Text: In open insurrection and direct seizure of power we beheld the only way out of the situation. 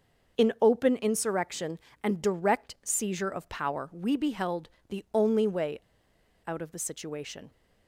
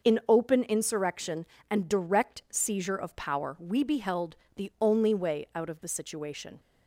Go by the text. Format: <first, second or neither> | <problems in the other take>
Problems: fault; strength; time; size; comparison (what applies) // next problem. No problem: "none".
second | starts louder than the rest; noticeable; until 1.4 s; 6 dB // pauses between "beheld" and "the"; slight; at 4.6 s; 0.22 s long; slight in the second // pauses between "way" and "out"; noticeable; at 5.7 s; 0.67 s long